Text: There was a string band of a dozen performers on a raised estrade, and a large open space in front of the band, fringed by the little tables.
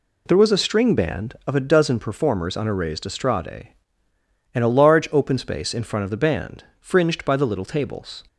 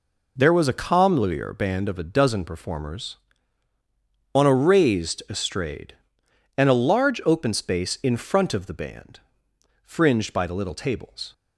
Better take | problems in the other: first | says "comlier" for "string"; at 0.7 s

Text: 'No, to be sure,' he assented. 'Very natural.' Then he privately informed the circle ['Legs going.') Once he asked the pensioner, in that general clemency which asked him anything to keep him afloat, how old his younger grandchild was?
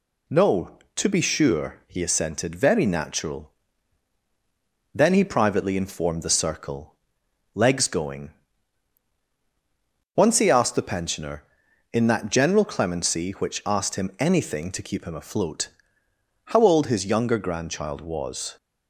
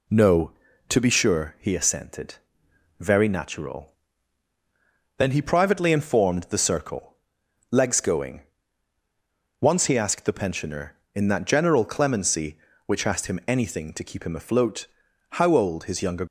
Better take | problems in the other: first | pauses between "circle" and "Legs"; noticeable; at 7.1 s; 0.54 s long; noticeable in the first // stops before "grandchild was"; at 16.2 s

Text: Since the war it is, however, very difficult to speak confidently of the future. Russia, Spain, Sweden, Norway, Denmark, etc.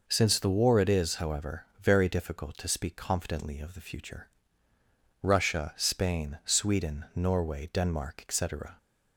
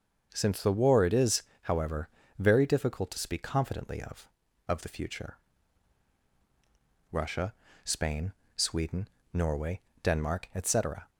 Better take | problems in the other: first | starts louder than the rest; until 1.3 s; 6.5 dB // says "of" twice; at 4.6 s

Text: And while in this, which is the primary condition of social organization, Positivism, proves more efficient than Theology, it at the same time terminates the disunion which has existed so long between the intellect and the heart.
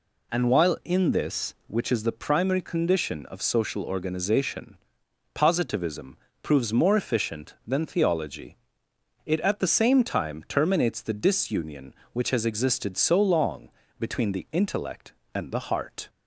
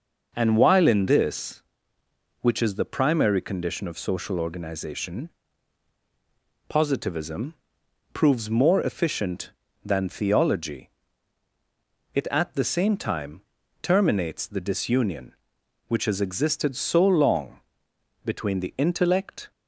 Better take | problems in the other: first | pauses between "time" and "terminates"; at 13.4 s; 0.42 s long // pauses between "long" and "between"; noticeable; at 17.5 s; 0.66 s long; slight in the first // stops before "and the heart"; at 19.5 s

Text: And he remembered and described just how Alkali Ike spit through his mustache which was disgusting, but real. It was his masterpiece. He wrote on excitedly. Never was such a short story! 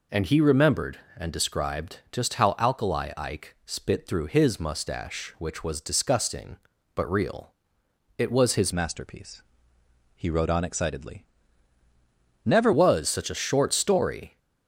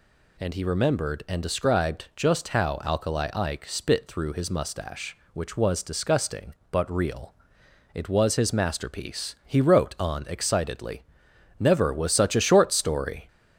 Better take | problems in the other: second | changes voice from "masterpiece" to "Never"; from 8.7 to 12.7 s; 4.0 s long

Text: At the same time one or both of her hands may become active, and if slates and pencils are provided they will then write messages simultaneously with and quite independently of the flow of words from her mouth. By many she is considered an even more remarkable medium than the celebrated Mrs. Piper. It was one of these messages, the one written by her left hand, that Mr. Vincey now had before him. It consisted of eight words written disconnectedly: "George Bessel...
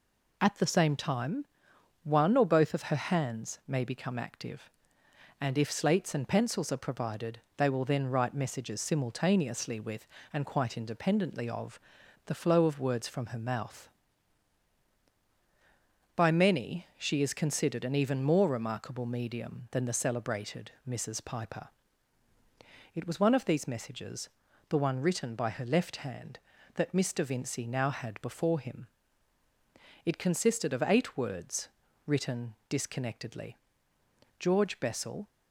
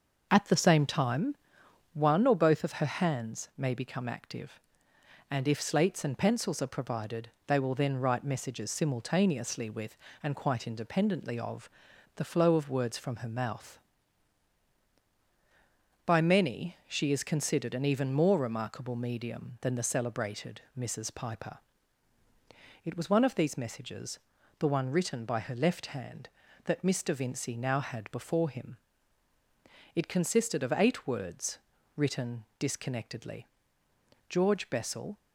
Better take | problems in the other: first | starts louder than the rest; noticeable; until 2.0 s; 6 dB // pauses between "time" and "one"; noticeable; at 1.3 s; 0.58 s long; noticeable in the first // pauses between "provided" and "they"; slight; at 7.2 s; 0.18 s long; slight in the first // pauses between "of" and "the"; noticeable; at 11.6 s; 0.46 s long; noticeable in the first // pauses between "words" and "written"; at 31.5 s; 0.40 s long; also in the first // pauses between "written" and "disconnectedly"; slight; at 32.4 s; 0.16 s long; slight in the first

